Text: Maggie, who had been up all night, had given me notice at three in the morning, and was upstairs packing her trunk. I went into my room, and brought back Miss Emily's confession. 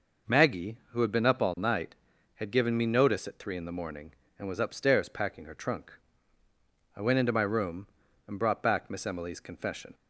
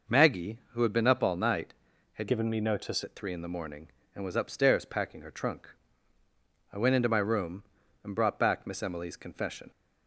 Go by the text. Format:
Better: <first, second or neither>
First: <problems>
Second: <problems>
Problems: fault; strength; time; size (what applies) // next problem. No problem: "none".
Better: first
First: none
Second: changes voice from "given" to "notice"; from 2.2 to 3.0 s; 0.8 s long